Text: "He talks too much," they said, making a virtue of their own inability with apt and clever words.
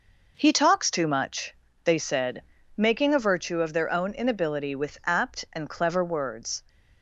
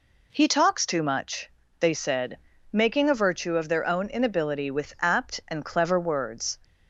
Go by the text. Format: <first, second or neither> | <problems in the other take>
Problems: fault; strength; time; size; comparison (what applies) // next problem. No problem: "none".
second | gets quieter; throughout; 6.5 dB